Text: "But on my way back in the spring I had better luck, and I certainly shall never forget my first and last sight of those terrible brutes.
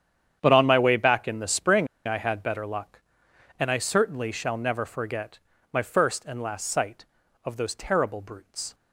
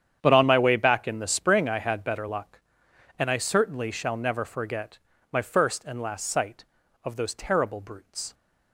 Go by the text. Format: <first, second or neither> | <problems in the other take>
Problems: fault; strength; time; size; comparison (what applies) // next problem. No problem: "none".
second | starts louder than the rest; strong; until 1.4 s; 9 dB; strong in the second // pauses between "spring" and "I"; slight; at 1.8 s; 0.21 s long // pauses between "forget" and "my"; slight; at 5.3 s; 0.34 s long; slight in the second